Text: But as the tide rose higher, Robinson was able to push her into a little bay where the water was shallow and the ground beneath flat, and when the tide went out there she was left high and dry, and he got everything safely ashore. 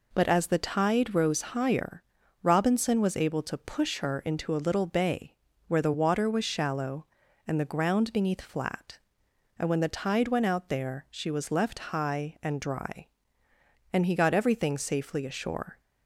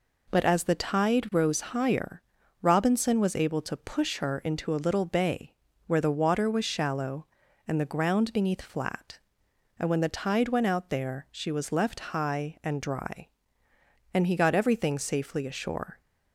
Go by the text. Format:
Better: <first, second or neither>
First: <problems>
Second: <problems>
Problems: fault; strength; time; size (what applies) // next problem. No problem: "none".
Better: neither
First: pauses between "bay" and "where"; slight; at 5.3 s; 0.32 s long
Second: pauses between "bay" and "where"; slight; at 5.5 s; 0.32 s long